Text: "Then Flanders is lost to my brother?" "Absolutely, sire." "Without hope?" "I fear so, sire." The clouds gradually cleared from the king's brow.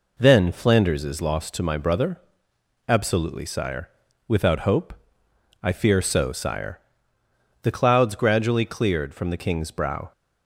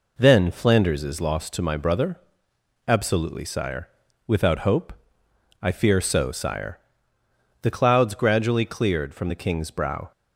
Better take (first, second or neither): neither